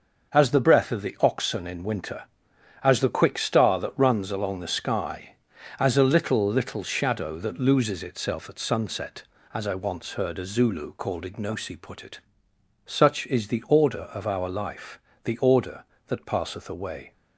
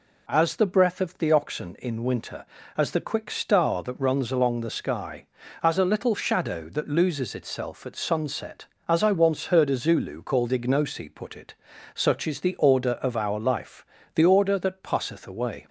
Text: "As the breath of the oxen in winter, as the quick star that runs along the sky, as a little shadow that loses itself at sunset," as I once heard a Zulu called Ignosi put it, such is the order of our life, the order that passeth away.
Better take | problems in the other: second | starts louder than the rest; until 1.3 s; 6 dB // says "little" twice; at 6.4 s

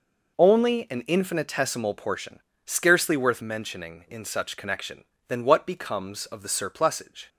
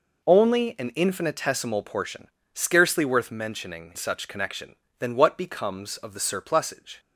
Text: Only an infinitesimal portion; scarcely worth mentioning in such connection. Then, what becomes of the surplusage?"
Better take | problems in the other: first | skips "in"; at 3.9 s

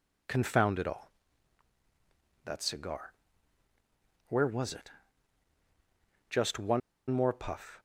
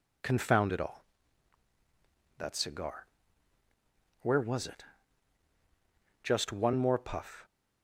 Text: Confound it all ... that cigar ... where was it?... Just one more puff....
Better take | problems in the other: second | pauses between "one" and "more"; slight; at 6.8 s; 0.29 s long

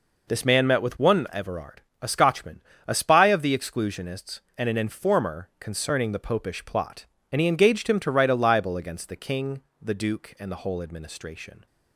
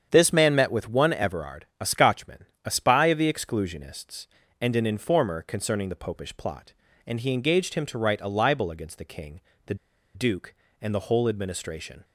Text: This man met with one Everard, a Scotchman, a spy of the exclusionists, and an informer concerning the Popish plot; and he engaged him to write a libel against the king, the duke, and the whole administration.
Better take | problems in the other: first | starts louder than the rest; strong; until 1.1 s; 8 dB // pauses between "the" and "duke"; at 9.7 s; 0.39 s long

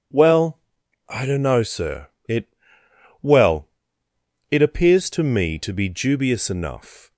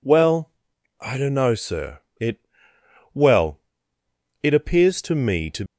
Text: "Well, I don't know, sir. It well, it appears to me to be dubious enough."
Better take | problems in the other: first | pauses between "It" and "well"; noticeable; at 2.4 s; 0.68 s long; noticeable in the first // stops before "be dubious enough"; at 5.6 s

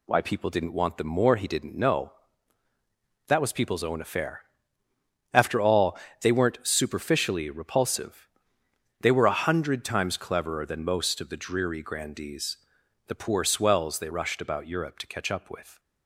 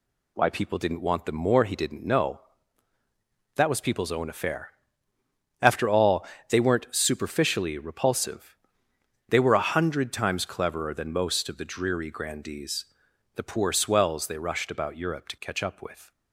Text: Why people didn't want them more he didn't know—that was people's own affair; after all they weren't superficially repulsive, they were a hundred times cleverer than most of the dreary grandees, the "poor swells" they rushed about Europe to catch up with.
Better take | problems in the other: neither | pauses between "all" and "they"; slight; the same in both

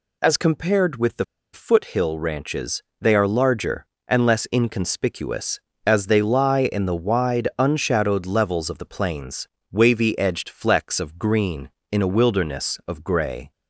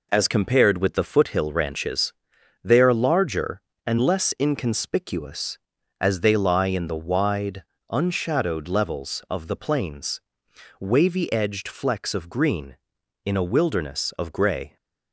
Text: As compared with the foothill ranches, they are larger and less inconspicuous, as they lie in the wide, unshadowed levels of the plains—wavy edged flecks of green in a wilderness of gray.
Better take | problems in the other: second | pauses between "the" and "foothill"; slight; at 1.2 s; 0.28 s long

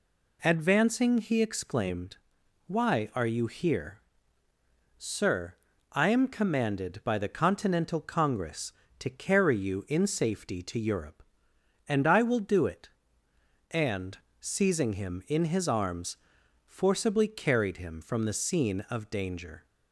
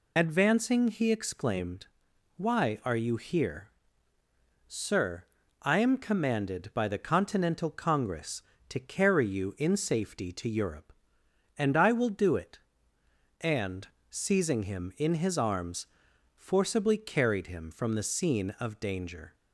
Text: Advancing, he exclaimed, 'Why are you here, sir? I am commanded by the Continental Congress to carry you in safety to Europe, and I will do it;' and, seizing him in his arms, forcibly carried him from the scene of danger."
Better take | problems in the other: first | loses the start of "Advancing"; at 0.1 s; 60 ms

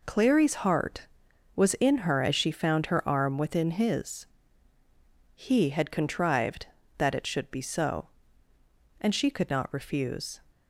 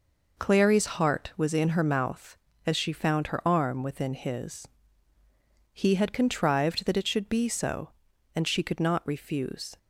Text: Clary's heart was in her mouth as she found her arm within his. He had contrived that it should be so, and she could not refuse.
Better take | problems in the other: second | skips "mouth"; at 2.2 s

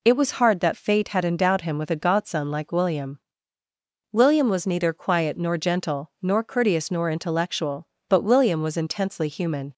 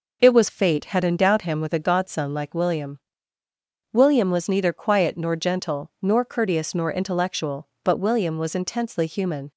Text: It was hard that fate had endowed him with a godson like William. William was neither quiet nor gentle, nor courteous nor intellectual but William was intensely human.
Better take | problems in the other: first | skips "hard that"; at 0.4 s

